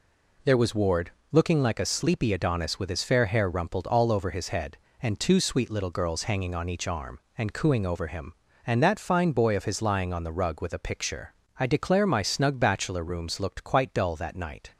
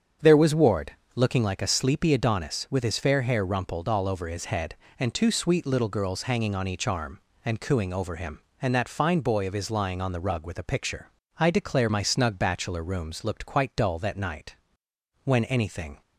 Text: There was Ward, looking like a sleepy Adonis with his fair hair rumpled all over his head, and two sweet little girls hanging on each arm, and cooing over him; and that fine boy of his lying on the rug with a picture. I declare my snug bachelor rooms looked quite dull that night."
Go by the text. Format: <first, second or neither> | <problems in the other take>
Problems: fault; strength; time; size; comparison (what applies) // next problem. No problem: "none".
first | starts louder than the rest; strong; until 1.4 s; 7.5 dB // goes on to say "When anything"; noticeable; from 15.2 s on; 0.78 s long